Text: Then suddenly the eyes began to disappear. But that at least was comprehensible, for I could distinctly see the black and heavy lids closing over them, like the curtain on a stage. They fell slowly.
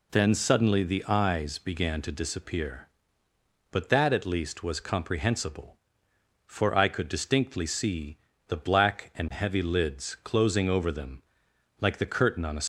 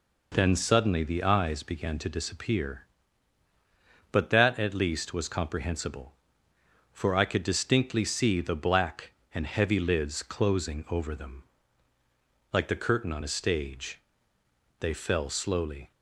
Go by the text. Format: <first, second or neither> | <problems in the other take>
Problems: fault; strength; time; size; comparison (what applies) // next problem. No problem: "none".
second | pauses between "see" and "the"; slight; at 8.1 s; 0.30 s long // stops before "stage They fell slowly"; at 12.6 s